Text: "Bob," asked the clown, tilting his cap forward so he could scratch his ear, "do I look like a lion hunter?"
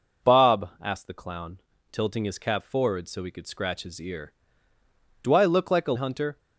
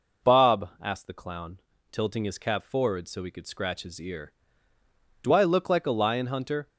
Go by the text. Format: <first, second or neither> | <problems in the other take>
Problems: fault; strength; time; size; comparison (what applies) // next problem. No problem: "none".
second | skips "lion"; at 5.9 s